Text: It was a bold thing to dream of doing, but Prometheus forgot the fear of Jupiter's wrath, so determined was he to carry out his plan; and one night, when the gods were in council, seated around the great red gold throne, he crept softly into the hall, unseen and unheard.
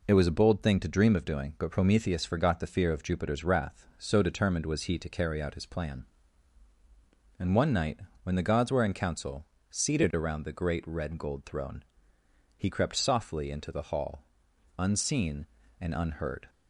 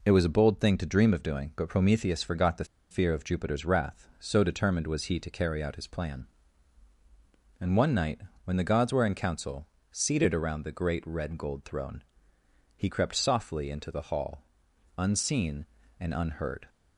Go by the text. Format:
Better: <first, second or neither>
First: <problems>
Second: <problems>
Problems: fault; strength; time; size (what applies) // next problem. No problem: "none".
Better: first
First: none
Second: pauses between "the" and "fear"; slight; at 2.6 s; 0.25 s long